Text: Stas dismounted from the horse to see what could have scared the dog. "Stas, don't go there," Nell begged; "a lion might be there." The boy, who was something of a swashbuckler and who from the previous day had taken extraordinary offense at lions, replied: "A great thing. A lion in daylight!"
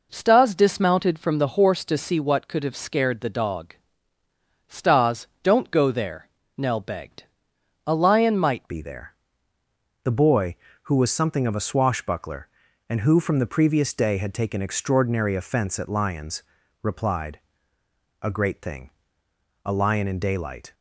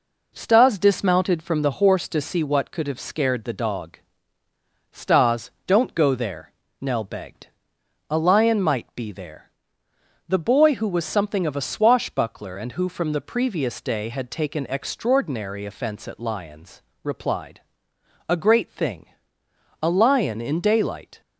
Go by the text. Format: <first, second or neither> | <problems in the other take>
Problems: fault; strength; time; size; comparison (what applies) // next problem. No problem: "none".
second | changes voice at "be"; from 8.6 s on; 12.1 s long